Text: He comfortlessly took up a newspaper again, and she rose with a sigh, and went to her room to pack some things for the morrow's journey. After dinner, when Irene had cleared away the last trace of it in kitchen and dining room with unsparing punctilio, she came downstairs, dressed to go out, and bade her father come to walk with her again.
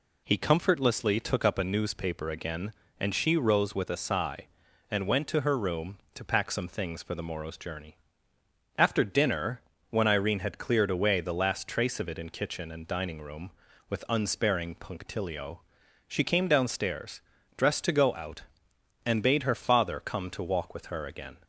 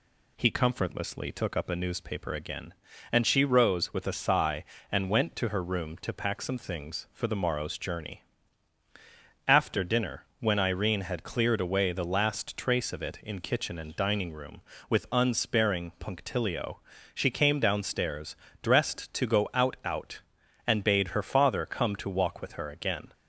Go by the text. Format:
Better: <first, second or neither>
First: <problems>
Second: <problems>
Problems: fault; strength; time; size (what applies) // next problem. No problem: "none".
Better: first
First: none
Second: says "out" twice; at 19.8 s